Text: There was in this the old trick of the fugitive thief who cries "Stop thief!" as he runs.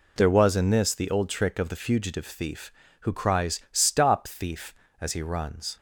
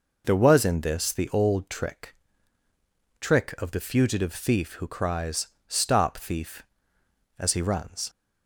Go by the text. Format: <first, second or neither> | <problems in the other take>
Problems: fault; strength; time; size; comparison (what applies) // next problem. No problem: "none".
first | says "trick" twice; at 3.1 s // pauses between "cries" and "Stop"; slight; at 5.4 s; 0.20 s long